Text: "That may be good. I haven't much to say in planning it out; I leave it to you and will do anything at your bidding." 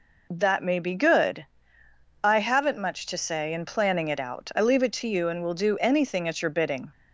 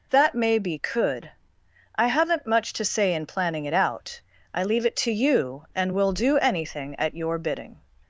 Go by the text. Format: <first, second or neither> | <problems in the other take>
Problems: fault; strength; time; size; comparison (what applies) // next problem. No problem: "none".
first | says "could" for "good"; at 0.7 s